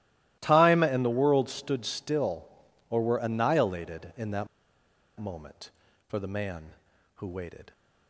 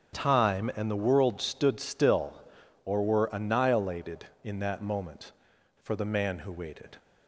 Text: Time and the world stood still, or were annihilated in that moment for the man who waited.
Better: second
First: starts louder than the rest; strong; until 1.4 s; 16 dB // pauses between "that" and "moment"; noticeable; at 4.4 s; 0.72 s long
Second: starts louder than the rest; strong; until 1.2 s; 7 dB

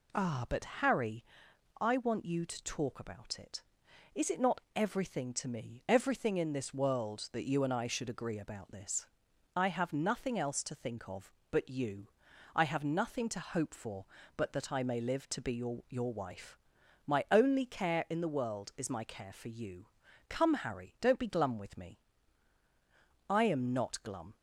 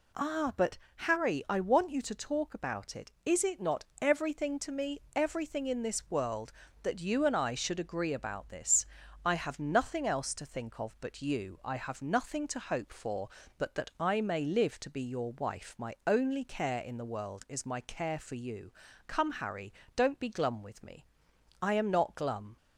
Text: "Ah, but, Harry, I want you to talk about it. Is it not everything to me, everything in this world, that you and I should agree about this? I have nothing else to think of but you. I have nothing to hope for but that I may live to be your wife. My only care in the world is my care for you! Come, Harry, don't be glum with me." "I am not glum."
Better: second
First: pauses between "not" and "everything"; slight; at 4.5 s; 0.16 s long // says "your" twice; at 15.8 s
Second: none

